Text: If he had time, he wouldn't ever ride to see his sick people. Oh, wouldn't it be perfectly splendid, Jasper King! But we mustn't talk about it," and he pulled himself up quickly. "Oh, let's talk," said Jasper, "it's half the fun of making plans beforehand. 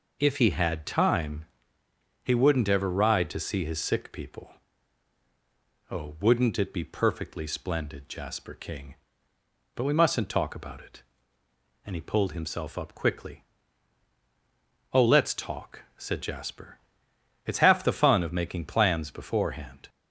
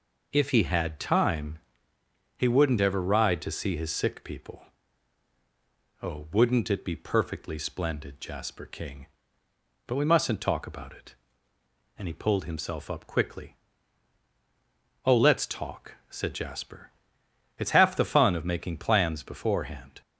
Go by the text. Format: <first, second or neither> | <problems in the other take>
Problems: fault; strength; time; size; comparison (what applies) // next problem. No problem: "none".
neither | none